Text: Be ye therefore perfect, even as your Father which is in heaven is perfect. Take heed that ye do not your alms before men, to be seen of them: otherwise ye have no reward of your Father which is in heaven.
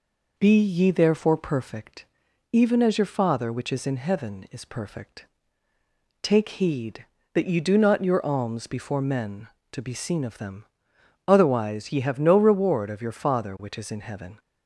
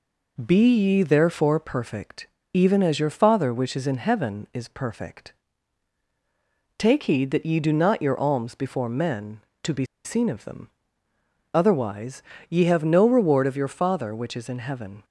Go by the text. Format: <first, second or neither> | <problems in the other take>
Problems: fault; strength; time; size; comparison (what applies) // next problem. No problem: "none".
first | pauses between "be" and "seen"; slight; at 9.8 s; 0.20 s long // pauses between "otherwise" and "ye"; slight; at 12.2 s; 0.30 s long